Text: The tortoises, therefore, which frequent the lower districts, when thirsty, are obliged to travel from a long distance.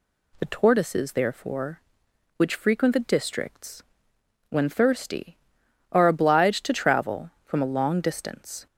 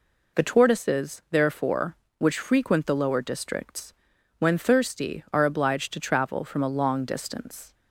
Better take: second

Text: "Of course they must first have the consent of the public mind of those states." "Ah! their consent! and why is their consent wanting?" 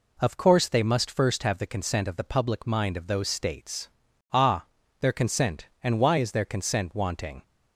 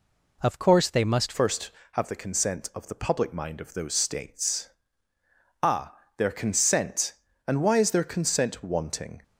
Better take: first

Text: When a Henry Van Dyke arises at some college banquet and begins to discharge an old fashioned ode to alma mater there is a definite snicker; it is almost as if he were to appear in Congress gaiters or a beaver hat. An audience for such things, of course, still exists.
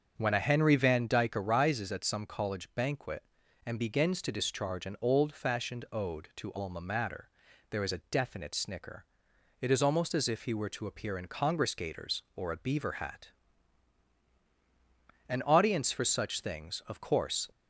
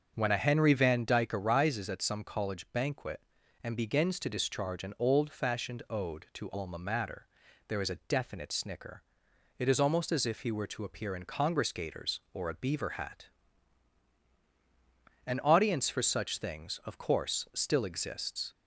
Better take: second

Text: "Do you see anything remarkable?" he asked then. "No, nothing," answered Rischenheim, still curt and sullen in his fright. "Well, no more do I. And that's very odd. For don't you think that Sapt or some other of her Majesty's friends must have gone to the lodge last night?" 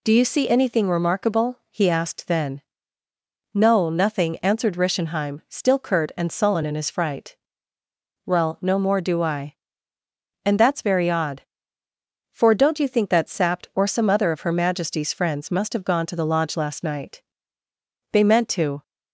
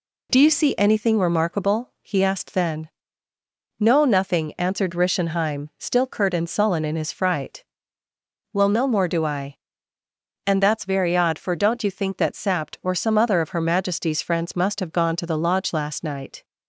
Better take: second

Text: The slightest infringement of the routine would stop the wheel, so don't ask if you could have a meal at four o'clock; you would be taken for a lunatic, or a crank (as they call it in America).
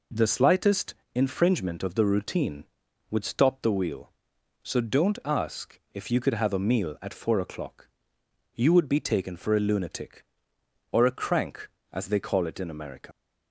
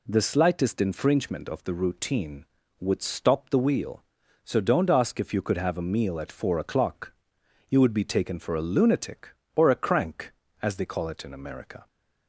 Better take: second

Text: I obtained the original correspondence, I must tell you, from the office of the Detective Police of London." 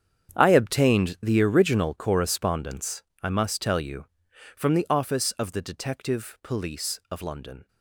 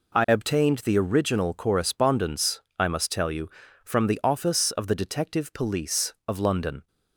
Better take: second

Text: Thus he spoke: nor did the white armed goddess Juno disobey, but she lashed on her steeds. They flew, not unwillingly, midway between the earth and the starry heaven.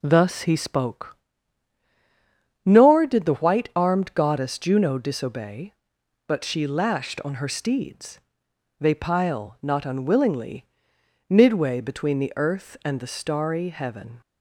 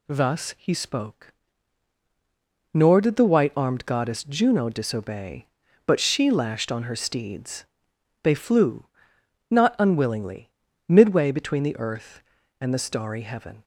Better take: second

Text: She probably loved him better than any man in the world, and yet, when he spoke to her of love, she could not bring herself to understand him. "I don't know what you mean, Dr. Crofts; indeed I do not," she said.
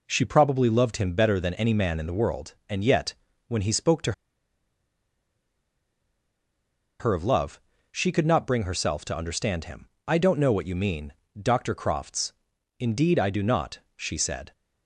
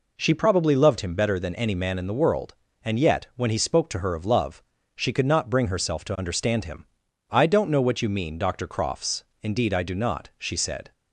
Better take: second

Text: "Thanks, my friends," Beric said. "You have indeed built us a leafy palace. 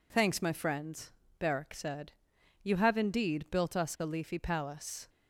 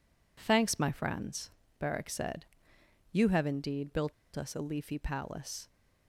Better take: first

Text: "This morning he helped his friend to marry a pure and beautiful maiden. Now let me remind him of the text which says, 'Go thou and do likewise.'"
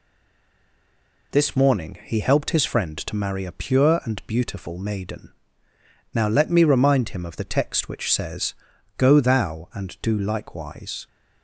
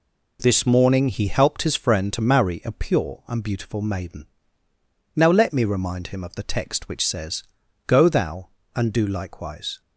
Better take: second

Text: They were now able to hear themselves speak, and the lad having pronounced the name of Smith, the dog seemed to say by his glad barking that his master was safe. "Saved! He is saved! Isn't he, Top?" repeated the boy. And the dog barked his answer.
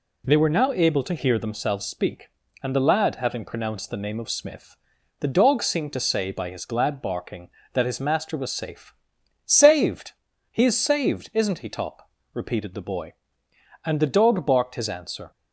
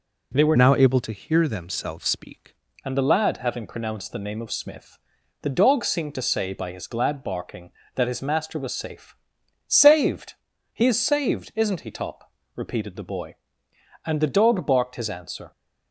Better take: first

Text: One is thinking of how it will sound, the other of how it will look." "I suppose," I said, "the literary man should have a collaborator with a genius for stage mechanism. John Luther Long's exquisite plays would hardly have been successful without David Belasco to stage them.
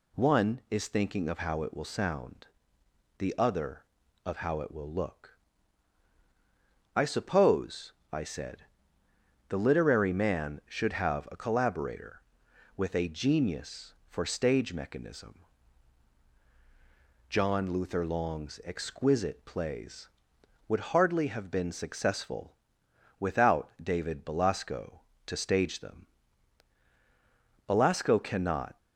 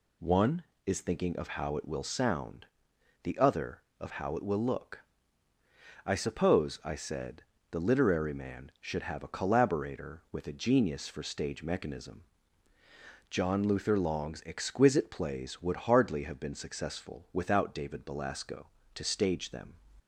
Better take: second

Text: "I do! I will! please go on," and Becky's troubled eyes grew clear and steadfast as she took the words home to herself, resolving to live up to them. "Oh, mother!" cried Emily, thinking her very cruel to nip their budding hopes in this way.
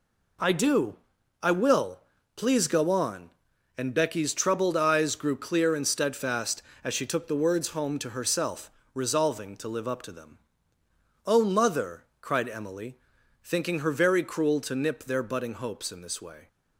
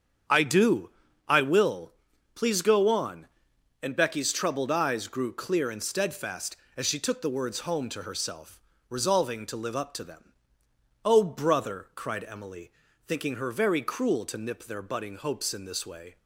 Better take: first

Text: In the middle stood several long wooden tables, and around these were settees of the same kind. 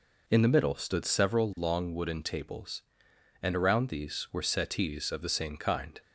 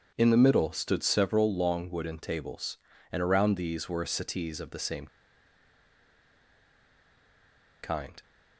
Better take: first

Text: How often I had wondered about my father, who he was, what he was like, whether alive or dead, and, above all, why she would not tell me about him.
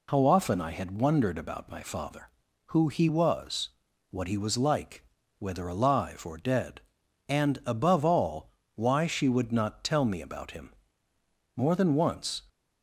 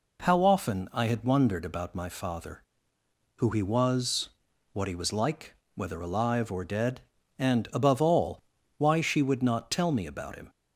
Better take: second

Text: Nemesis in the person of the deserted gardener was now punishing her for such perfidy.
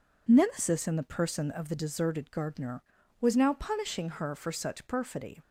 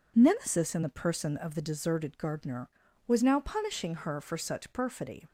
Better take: neither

